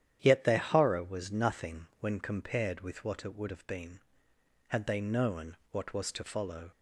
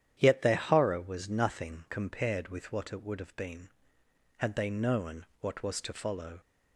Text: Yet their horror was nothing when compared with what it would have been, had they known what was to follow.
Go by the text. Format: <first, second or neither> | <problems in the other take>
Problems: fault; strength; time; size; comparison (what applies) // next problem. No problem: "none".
first | starts louder than the rest; strong; until 1.1 s; 10 dB; strong in the first // skips "when"; at 1.8 s // pauses between "known" and "what"; slight; at 5.2 s; 0.16 s long; slight in the first